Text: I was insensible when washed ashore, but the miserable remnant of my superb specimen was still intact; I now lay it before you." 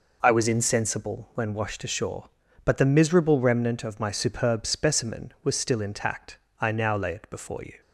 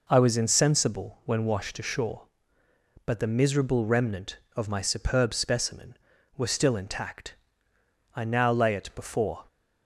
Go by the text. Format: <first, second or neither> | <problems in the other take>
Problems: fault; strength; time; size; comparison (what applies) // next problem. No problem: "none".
first | stops before "you"; at 9.4 s